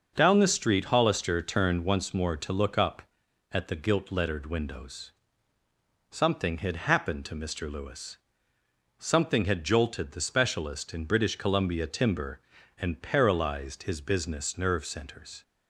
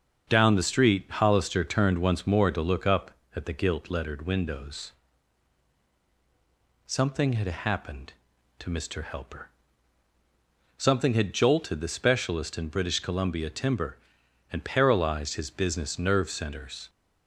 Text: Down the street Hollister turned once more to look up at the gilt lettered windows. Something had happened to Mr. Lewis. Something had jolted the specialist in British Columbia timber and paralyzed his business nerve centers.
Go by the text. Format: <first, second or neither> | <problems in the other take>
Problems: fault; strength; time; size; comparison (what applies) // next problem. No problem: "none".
first | starts louder than the rest; until 1.3 s; 6.5 dB; noticeable in the first // says "Helper" for "Lewis"; at 9.0 s